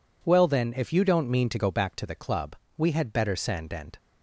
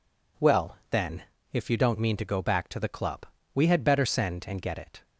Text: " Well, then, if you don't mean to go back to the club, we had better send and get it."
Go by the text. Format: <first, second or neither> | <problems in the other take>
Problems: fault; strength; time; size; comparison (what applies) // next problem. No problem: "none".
second | stops before "get it"; at 3.9 s